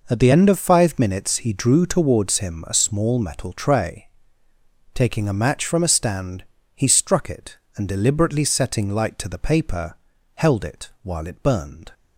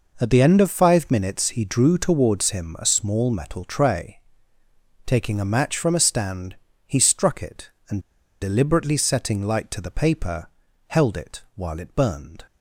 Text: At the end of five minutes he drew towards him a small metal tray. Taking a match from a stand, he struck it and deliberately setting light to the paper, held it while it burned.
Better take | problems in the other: first | pauses between "and" and "deliberately"; at 7.9 s; 0.41 s long

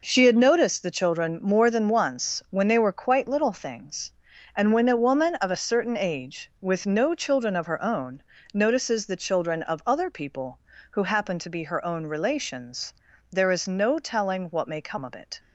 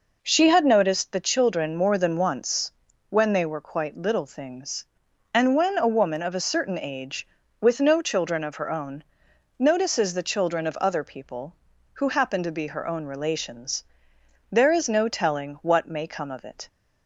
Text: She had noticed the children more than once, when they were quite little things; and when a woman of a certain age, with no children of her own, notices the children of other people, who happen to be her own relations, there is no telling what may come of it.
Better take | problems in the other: neither | none

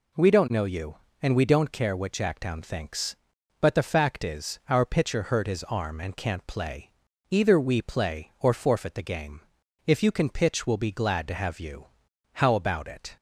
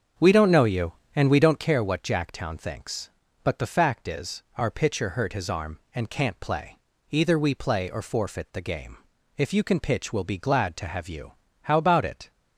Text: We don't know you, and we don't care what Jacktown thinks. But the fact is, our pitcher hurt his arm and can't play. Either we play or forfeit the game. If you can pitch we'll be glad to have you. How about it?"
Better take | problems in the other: first | starts louder than the rest; until 1.7 s; 7 dB

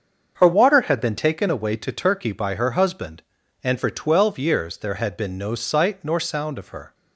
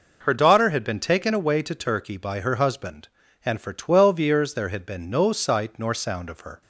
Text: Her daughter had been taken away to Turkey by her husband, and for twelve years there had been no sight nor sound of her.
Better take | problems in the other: second | starts louder than the rest; until 1.3 s; 7 dB // says "water" for "daughter"; at 0.4 s

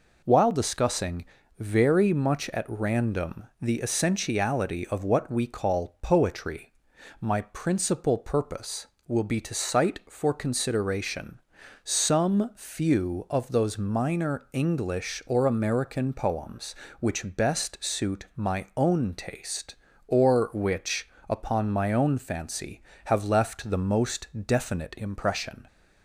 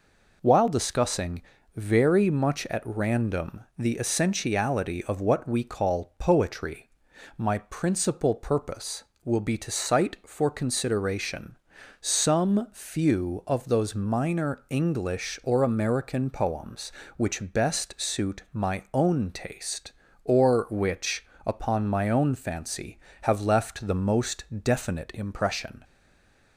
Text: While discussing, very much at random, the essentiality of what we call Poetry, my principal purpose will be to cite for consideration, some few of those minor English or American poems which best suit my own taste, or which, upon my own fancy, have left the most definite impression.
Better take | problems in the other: first | pauses between "most" and "definite"; slight; at 24.4 s; 0.20 s long; slight in the first // stays silent after the last word; slight; from 25.8 s on; 0.7 s long

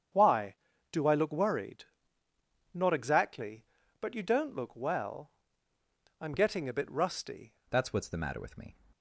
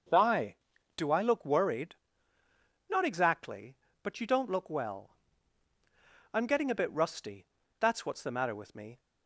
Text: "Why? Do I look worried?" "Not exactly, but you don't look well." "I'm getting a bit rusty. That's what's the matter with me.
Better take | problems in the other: second | starts louder than the rest; strong; until 1.4 s; 7.5 dB // changes voice at "That's"; from 7.7 s on; 1.0 s long

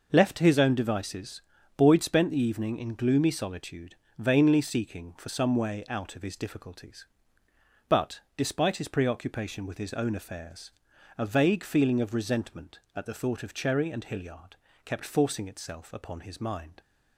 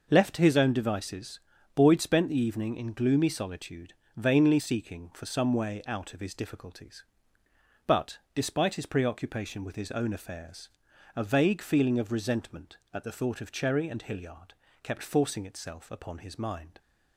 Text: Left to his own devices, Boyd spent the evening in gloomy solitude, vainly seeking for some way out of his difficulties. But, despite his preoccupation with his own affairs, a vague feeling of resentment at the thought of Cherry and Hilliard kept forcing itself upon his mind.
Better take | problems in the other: neither | pauses between "Hilliard" and "kept"; slight; the same in both

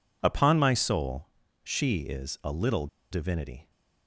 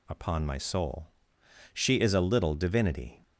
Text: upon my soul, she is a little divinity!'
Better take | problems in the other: second | pauses between "little" and "divinity"; slight; at 2.8 s; 0.25 s long

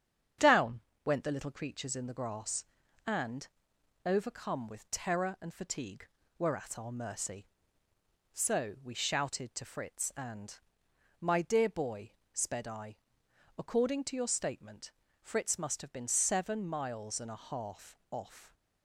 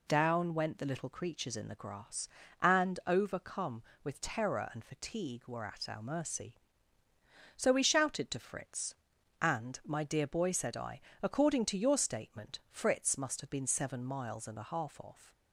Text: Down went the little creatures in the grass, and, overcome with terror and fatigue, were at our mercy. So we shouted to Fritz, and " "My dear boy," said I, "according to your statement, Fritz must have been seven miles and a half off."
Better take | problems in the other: second | starts louder than the rest; strong; until 1.6 s; 9 dB // pauses between "Down" and "went"; slight; at 0.7 s; 0.26 s long // says "sped" for "said"; at 12.3 s

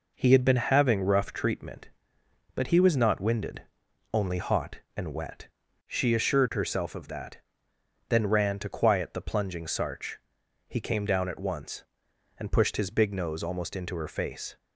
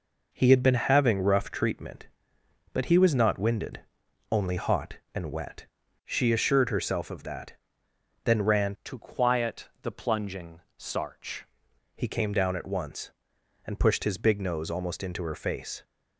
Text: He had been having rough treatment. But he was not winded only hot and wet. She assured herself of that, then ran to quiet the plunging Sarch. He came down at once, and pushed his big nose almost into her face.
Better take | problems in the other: first | pauses between "winded" and "only"; noticeable; at 3.8 s; 0.50 s long; noticeable in the first // changes voice from "to" to "Sarch"; from 8.8 to 11.4 s; 2.6 s long // pauses between "plunging" and "Sarch"; slight; at 10.6 s; 0.16 s long

